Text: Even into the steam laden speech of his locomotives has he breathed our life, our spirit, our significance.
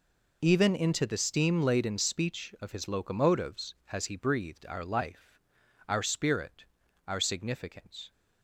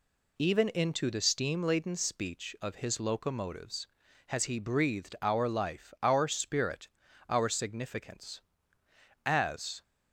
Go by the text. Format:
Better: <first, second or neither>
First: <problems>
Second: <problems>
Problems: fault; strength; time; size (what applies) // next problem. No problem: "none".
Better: first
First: none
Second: goes on to say "As"; from 9.2 s on; 0.58 s long